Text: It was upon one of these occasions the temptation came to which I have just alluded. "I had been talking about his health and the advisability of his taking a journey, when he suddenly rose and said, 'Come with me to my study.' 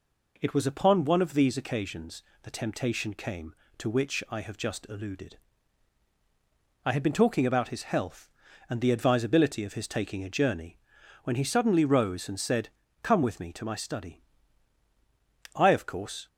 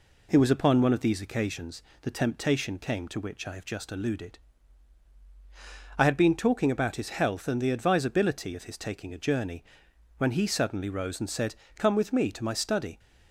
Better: second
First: pauses between "occasions" and "the"; slight; at 2.2 s; 0.20 s long // goes on to say "I of course"; noticeable; from 15.5 s on; 0.72 s long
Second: pauses between "occasions" and "the"; slight; at 1.8 s; 0.20 s long

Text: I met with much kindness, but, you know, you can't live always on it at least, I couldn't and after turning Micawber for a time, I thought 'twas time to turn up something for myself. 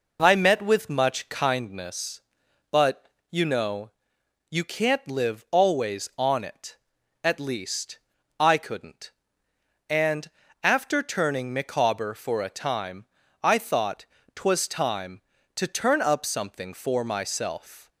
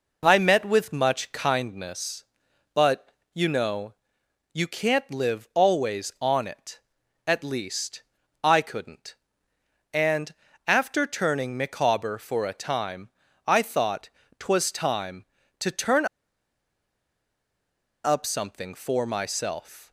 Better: first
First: pauses between "and" and "after"; slight; at 10.2 s; 0.32 s long // pauses between "thought" and "twas"; slight; at 14.0 s; 0.30 s long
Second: pauses between "and" and "after"; slight; at 10.3 s; 0.32 s long // pauses between "thought" and "twas"; slight; at 14.0 s; 0.30 s long // pauses between "turn" and "up"; strong; at 16.0 s; 1.9 s long

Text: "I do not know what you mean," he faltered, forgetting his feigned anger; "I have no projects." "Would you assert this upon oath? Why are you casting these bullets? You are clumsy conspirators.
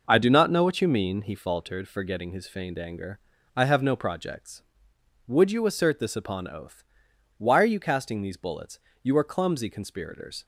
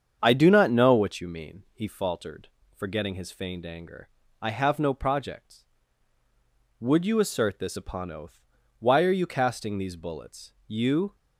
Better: first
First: none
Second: starts louder than the rest; strong; until 1.2 s; 7.5 dB // stops before "are clumsy conspirators"; at 11.1 s

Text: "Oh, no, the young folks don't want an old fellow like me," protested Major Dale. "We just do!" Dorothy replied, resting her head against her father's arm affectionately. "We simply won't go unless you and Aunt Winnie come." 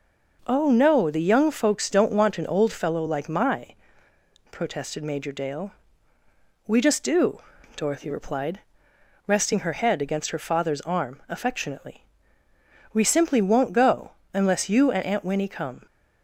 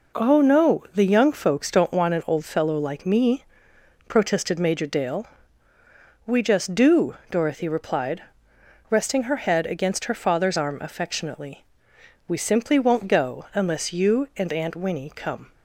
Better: second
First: says "my" for "me"; at 3.2 s // pauses between "go" and "unless"; slight; at 14.1 s; 0.22 s long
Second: none

